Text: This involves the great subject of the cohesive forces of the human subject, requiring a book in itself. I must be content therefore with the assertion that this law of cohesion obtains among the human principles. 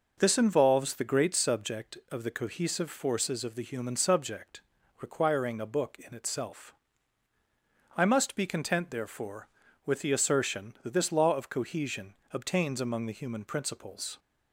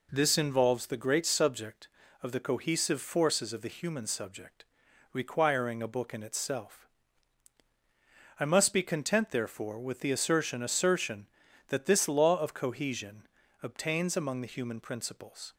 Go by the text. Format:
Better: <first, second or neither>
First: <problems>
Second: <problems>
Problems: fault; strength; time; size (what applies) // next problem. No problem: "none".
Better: first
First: pauses between "cohesion" and "obtains"; slight; at 12.1 s; 0.18 s long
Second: says "assertion" twice; at 10.6 s // pauses between "cohesion" and "obtains"; at 13.2 s; 0.38 s long